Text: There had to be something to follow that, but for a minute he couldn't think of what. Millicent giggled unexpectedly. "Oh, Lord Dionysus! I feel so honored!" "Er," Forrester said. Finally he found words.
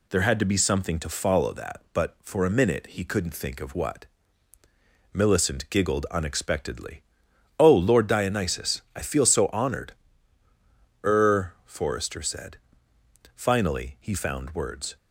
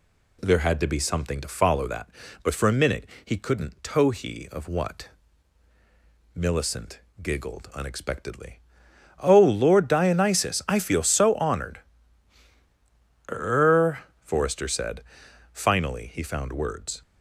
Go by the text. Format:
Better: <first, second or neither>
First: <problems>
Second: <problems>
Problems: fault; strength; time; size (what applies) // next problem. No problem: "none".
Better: first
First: none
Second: pauses between "minute" and "he"; slight; at 3.0 s; 0.18 s long // says "tohi" for "think"; at 3.8 s // pauses between "Millicent" and "giggled"; slight; at 6.9 s; 0.22 s long